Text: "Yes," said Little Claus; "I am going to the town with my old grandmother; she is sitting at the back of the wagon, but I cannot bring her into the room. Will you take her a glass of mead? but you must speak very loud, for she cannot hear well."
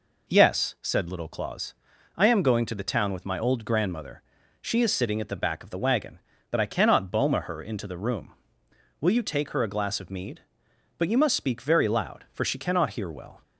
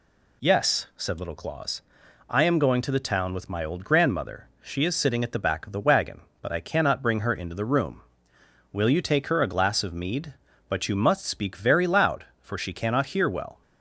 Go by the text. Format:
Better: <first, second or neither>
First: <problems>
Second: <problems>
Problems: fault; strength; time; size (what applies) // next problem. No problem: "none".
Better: second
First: says "boma" for "bring"; at 7.0 s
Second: none